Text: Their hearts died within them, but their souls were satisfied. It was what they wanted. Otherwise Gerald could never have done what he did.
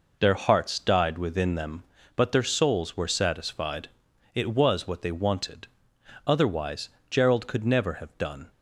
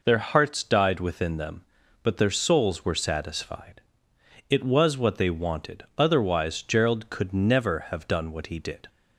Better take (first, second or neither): second